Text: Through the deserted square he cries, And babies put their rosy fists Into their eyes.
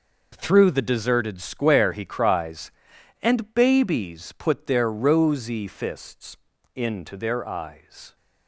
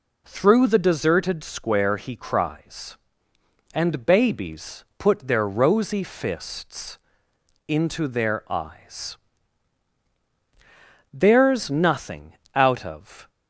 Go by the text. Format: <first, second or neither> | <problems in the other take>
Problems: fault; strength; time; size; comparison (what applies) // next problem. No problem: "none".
first | pauses between "fists" and "Into"; noticeable; at 6.9 s; 0.70 s long; also in the first // goes on to say "There's nothing out of"; strong; from 11.1 s on; 2.1 s long